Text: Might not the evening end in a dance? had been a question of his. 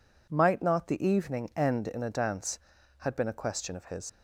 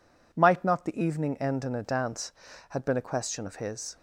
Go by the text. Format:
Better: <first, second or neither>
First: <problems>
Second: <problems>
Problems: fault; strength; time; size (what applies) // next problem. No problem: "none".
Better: second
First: leaves "his" unfinished; at 4.0 s; 80 ms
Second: none